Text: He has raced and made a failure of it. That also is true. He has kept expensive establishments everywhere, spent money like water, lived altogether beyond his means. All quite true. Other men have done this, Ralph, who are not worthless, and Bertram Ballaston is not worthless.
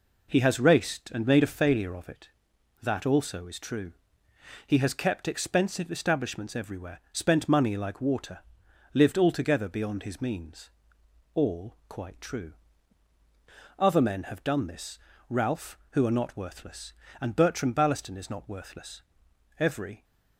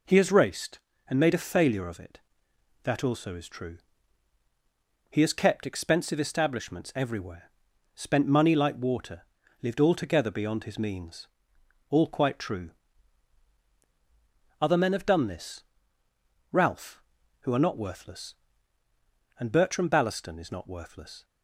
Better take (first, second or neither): second